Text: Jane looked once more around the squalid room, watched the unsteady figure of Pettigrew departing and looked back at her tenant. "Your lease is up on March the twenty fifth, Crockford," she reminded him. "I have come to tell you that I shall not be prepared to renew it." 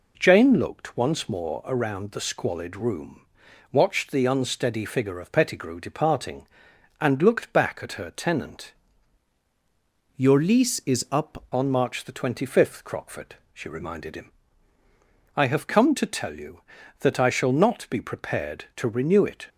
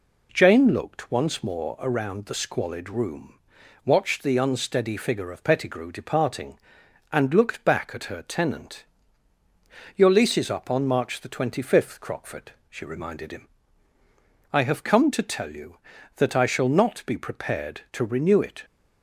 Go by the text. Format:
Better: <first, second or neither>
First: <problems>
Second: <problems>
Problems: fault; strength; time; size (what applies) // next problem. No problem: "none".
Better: second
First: changes voice from "Your" to "up"; from 10.1 to 11.4 s; 1.3 s long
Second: none